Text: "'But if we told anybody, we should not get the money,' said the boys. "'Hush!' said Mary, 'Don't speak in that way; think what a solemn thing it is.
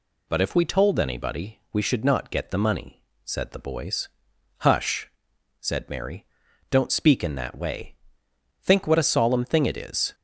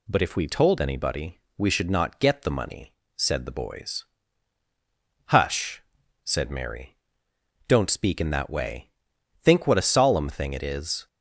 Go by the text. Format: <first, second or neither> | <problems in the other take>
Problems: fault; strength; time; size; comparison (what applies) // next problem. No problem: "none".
neither | none